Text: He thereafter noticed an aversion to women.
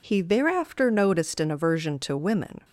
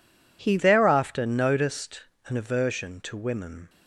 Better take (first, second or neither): first